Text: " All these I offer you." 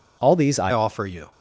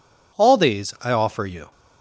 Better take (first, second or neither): second